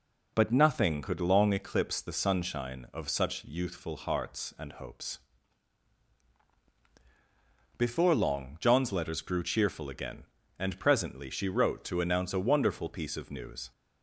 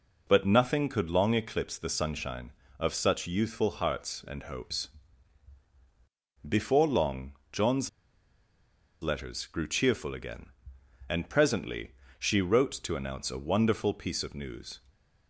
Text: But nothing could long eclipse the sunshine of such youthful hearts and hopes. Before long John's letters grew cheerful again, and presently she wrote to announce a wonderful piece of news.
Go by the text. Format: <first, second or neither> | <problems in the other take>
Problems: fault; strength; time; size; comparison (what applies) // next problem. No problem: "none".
first | pauses between "long" and "John's"; slight; at 7.3 s; 0.18 s long // pauses between "John's" and "letters"; at 7.8 s; 1.1 s long // pauses between "presently" and "she"; slight; at 11.9 s; 0.26 s long